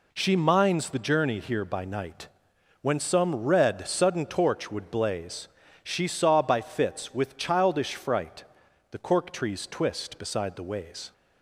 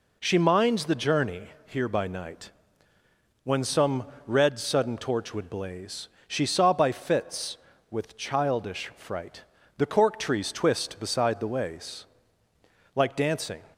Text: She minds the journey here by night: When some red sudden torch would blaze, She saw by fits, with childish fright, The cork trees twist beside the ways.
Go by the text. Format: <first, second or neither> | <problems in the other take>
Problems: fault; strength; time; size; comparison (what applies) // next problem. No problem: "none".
first | pauses between "journey" and "here"; slight; at 1.4 s; 0.18 s long // pauses between "some" and "red"; slight; at 4.0 s; 0.18 s long // goes on to say "Like dancing"; noticeable; from 12.9 s on; 0.66 s long